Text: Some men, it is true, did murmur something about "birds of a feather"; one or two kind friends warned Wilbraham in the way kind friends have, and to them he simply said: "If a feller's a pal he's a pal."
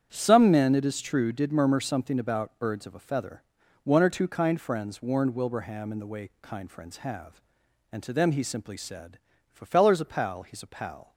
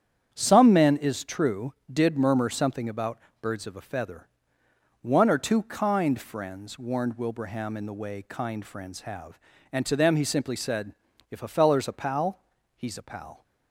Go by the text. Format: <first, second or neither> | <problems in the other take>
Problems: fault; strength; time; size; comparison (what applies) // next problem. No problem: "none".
first | starts louder than the rest; strong; until 1.3 s; 8.5 dB; strong in the first // skips "it"; at 0.9 s // pauses between "about" and "birds"; slight; at 3.1 s; 0.22 s long // pauses between "pal" and "he's"; slight; at 12.3 s; 0.36 s long